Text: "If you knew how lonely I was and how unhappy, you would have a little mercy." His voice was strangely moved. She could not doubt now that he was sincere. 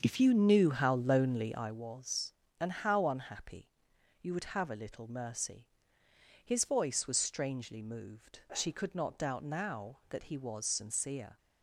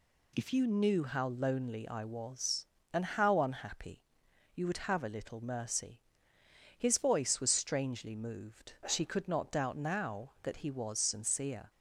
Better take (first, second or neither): second